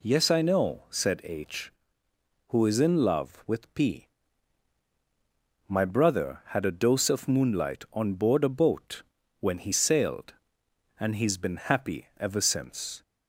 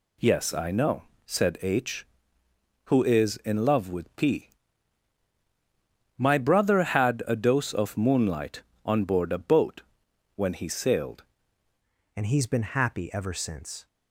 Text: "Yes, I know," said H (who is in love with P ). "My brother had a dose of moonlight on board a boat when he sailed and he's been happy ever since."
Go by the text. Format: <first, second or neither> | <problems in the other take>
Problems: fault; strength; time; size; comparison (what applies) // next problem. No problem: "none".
first | pauses between "boat" and "when"; noticeable; at 9.8 s; 0.52 s long; also in the first // changes voice at "and"; from 12.1 s on; 1.7 s long